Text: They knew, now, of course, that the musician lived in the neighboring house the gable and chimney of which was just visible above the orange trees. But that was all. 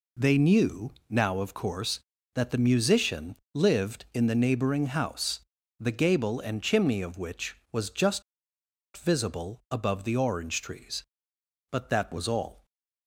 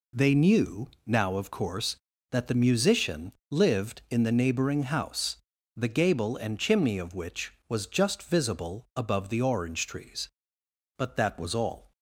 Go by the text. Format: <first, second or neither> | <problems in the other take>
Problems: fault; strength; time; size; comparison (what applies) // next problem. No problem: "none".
second | pauses between "musician" and "lived"; slight; at 3.3 s; 0.18 s long; slight in the second // pauses between "house" and "the"; at 5.3 s; 0.40 s long; also in the second // pauses between "just" and "visible"; noticeable; at 8.2 s; 0.74 s long